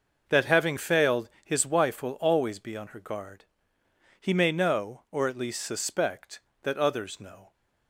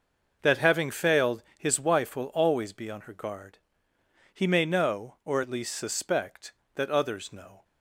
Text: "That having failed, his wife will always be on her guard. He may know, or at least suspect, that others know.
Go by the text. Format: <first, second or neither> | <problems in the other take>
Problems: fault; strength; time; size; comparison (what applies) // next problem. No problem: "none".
neither | none